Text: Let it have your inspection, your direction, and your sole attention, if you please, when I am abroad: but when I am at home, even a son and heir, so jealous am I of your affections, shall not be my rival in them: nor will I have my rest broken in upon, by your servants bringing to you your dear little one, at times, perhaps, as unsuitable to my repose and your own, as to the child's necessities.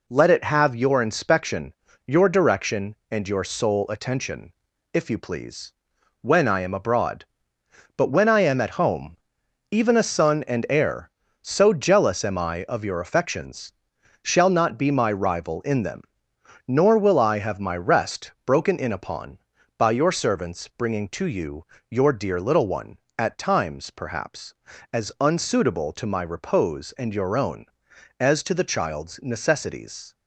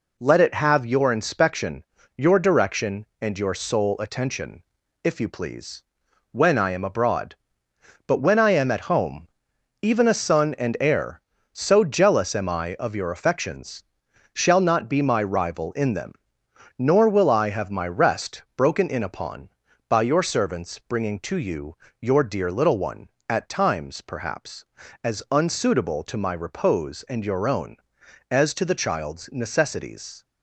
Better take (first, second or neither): neither